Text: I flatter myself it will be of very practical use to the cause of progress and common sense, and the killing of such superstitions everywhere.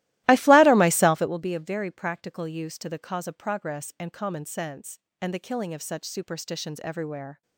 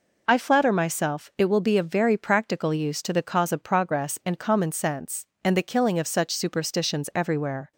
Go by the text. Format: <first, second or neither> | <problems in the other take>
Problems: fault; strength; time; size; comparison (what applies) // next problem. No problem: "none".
second | starts louder than the rest; strong; until 1.5 s; 17 dB